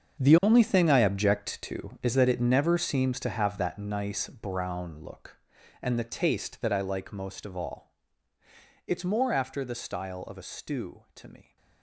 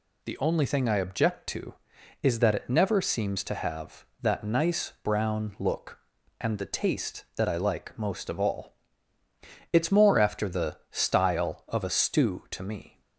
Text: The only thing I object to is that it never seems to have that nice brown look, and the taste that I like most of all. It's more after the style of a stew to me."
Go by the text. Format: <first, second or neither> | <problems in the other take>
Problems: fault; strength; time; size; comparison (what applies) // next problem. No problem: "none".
second | gets quieter; strong; throughout; 13.5 dB